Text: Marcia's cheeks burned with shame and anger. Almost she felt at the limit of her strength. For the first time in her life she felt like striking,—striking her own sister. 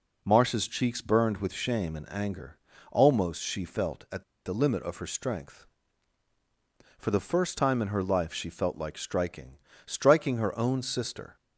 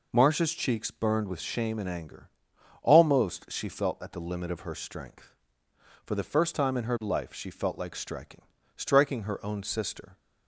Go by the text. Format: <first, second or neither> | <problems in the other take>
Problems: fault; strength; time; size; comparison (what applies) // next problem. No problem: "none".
second | pauses between "at" and "the"; slight; at 4.2 s; 0.23 s long